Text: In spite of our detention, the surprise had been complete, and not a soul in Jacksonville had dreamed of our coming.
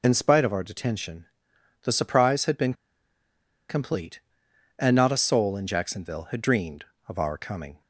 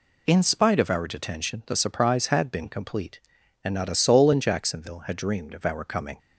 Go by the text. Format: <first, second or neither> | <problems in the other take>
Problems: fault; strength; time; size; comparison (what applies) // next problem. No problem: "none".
second | pauses between "been" and "complete"; noticeable; at 2.7 s; 0.96 s long